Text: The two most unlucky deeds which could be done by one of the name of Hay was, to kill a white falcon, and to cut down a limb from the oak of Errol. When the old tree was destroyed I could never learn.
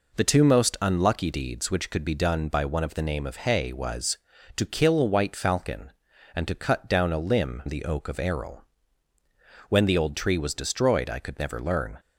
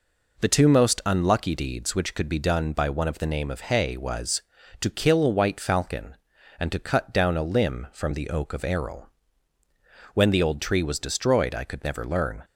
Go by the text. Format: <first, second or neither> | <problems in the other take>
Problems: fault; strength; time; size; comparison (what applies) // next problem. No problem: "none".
second | skips "from"; at 7.6 s